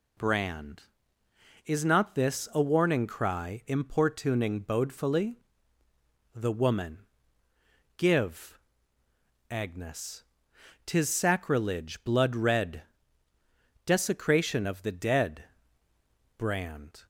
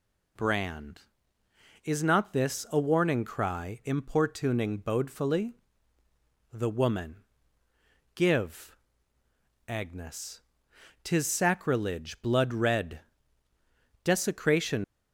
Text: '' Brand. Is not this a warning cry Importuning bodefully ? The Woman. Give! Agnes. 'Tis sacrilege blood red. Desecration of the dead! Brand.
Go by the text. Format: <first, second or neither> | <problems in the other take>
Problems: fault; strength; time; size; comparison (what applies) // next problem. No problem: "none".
first | stops before "of the dead Brand"; at 14.8 s